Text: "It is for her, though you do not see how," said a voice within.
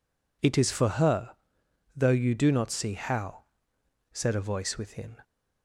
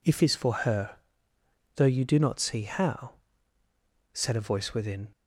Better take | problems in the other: first | says "If" for "It"; at 0.0 s

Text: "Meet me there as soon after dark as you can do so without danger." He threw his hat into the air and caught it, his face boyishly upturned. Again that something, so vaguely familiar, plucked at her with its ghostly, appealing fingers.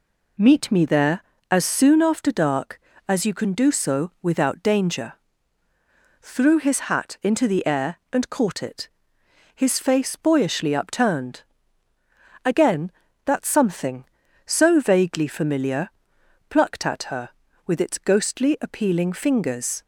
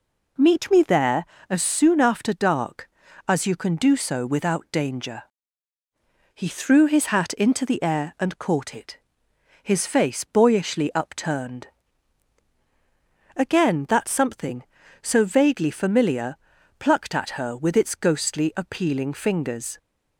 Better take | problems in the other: second | skips "He"; at 5.6 s

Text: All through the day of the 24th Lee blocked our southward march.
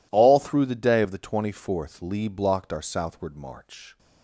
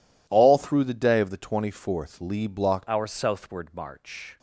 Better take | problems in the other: first | changes voice at "our"; from 2.8 s on; 1.5 s long

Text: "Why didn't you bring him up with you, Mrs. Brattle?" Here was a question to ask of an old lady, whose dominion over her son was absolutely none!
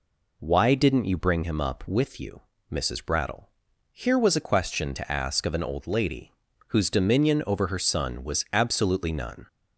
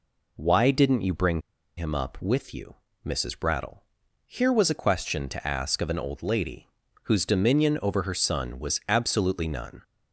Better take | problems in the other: first | pauses between "bring" and "him"; at 1.4 s; 0.37 s long

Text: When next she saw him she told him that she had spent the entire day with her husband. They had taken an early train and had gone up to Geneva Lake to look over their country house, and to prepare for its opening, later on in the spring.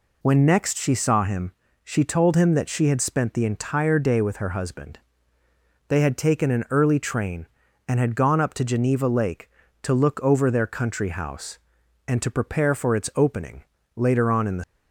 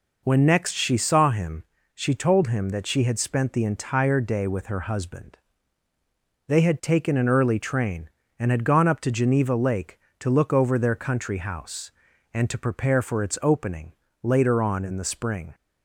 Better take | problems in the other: second | pauses between "him" and "she"; slight; at 1.5 s; 0.32 s long; slight in the second // stops before "spring"; at 14.6 s

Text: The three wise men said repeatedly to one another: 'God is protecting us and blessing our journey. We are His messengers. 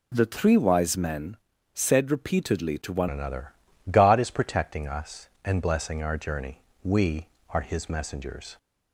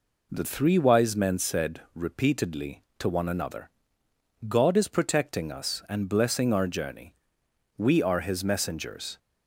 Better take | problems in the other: second | pauses between "men" and "said"; slight; at 1.3 s; 0.36 s long // changes voice at "another"; from 3.0 s on; 5.5 s long

